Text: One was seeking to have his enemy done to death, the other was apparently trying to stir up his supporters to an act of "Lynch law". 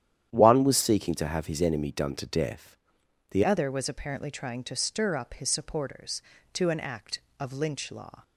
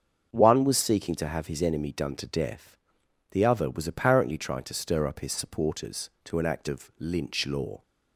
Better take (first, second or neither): second